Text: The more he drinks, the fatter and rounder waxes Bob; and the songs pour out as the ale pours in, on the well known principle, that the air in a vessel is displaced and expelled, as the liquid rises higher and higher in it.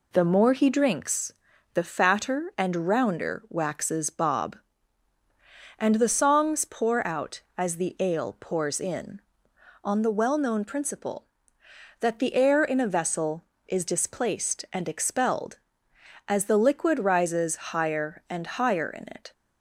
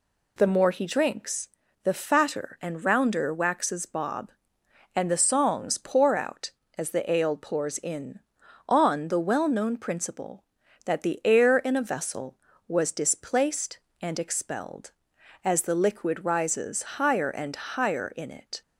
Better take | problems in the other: first | says "was" for "is"; at 12.6 s

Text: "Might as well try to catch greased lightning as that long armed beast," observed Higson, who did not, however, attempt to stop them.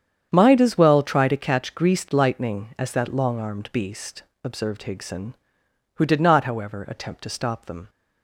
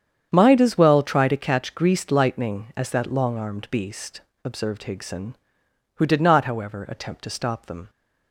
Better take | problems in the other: neither | starts louder than the rest; strong; the same in both

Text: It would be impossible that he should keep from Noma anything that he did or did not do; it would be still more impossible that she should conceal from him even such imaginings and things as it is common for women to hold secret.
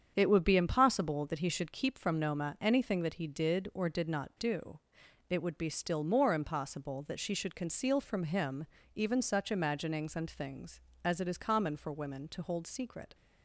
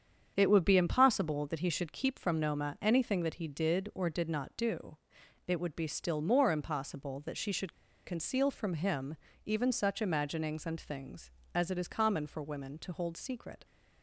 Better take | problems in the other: first | starts louder than the rest; strong; until 1.3 s; 7.5 dB; strong in the first // pauses between "should" and "conceal"; slight; at 7.7 s; 0.34 s long // pauses between "him" and "even"; slight; at 9.1 s; 0.30 s long; slight in the first

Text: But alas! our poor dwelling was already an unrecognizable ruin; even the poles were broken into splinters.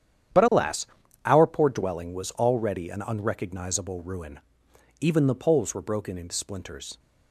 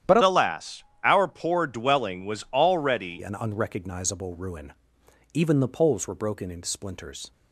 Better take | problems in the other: first | starts louder than the rest; strong; until 1.2 s; 10.5 dB; strong in the first // changes voice from "alas" to "already"; from 0.2 to 3.2 s; 3.0 s long

